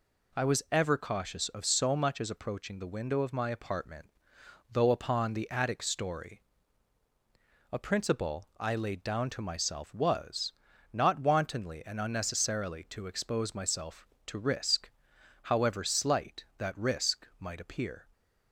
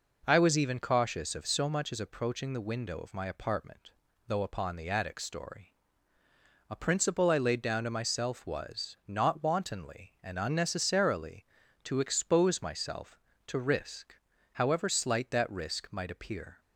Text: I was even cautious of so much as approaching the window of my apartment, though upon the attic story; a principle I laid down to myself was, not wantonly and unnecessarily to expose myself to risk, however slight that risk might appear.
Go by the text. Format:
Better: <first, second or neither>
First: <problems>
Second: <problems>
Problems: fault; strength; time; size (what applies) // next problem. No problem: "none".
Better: second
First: says "ever" for "even"; at 0.7 s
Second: none